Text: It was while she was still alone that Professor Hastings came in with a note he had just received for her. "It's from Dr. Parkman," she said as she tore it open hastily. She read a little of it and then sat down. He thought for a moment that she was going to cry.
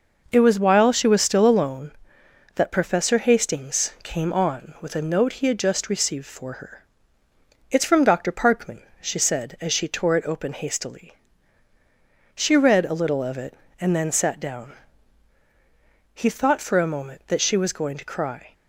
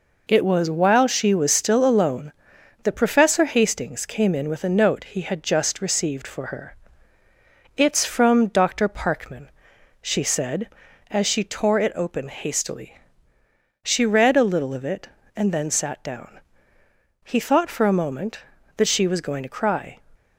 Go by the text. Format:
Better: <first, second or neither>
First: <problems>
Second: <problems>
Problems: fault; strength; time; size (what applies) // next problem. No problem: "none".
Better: second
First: says "on" for "in"; at 4.3 s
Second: none